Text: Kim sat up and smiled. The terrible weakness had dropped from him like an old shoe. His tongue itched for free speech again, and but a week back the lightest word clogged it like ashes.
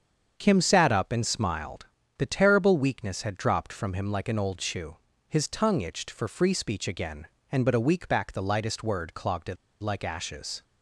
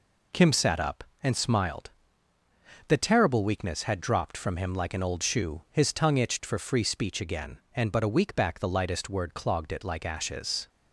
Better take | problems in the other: second | starts louder than the rest; strong; until 1.3 s; 7 dB // pauses between "it" and "like"; slight; at 9.5 s; 0.26 s long

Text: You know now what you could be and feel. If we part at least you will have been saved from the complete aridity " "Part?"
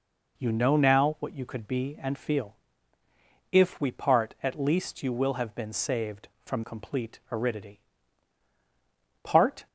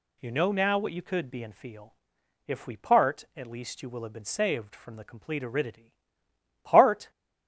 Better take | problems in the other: second | skips "the"; at 6.6 s

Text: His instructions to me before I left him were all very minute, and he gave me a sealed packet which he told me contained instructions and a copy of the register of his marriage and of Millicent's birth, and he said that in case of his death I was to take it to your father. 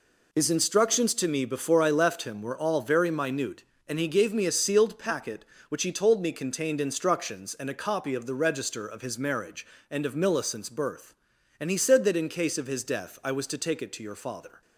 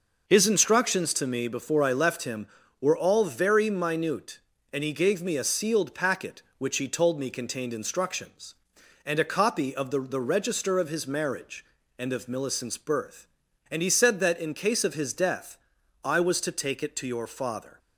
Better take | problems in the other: first | says "the" twice; at 10.0 s // pauses between "death" and "I"; at 15.5 s; 0.44 s long

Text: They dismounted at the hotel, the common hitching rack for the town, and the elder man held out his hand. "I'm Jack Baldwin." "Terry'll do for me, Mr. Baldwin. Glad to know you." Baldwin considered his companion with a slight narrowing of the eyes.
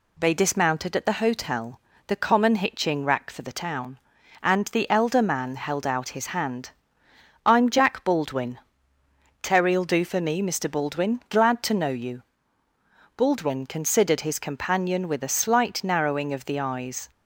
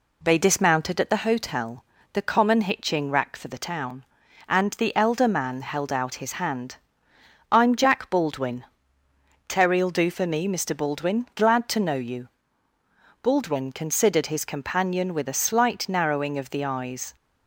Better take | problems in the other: first | starts louder than the rest; slight; until 1.2 s; 2.5 dB

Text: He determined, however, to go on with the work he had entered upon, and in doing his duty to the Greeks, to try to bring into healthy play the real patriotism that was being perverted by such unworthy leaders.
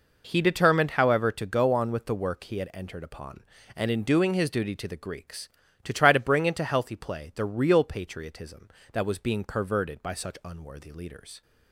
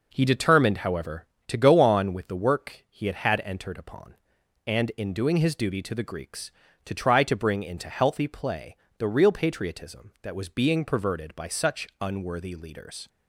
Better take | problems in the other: first | says "had" twice; at 3.1 s // pauses between "play" and "the"; slight; at 8.7 s; 0.22 s long

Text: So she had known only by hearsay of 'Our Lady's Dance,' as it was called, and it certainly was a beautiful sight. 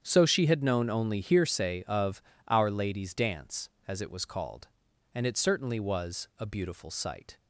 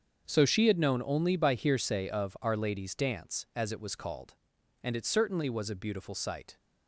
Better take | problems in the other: second | starts louder than the rest; strong; until 1.0 s; 8.5 dB; also in the second // skips "by"; at 1.2 s // pauses between "of" and "Our"; slight; at 2.2 s; 0.28 s long

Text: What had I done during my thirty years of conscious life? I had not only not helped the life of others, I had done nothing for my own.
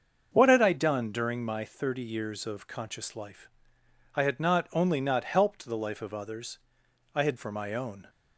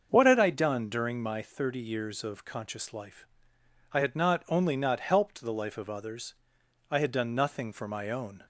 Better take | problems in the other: second | starts louder than the rest; until 1.3 s; 6.5 dB; also in the second // skips "done nothing"; at 7.3 s

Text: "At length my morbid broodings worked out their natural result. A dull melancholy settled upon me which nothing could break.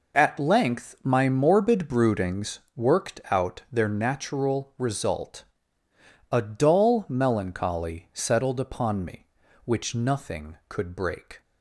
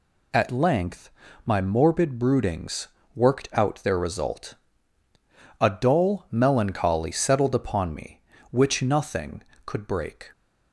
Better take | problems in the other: first | pauses between "length" and "my"; slight; at 1.0 s; 0.36 s long // pauses between "broodings" and "worked"; slight; at 2.8 s; 0.28 s long // skips "natural"; at 3.9 s

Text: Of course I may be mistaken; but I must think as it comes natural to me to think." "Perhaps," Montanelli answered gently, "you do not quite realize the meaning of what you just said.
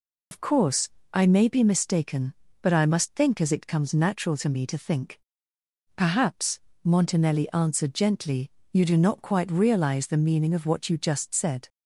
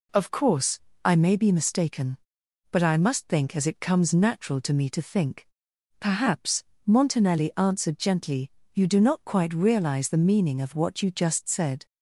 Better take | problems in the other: second | loses the start of "Of"; at 0.3 s; 70 ms // pauses between "course" and "I"; slight; at 0.8 s; 0.24 s long; slight in the second

